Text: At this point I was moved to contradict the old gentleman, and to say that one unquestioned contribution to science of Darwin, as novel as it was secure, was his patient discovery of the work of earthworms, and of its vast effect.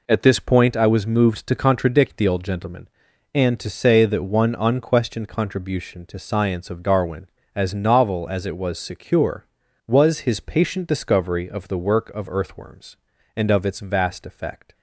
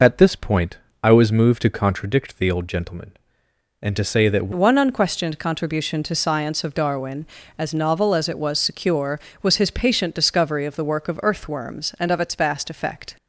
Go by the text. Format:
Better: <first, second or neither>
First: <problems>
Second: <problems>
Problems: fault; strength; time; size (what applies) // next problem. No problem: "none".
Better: first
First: none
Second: pauses between "point" and "I"; slight; at 0.7 s; 0.24 s long // changes voice at "one"; from 4.5 s on; 8.6 s long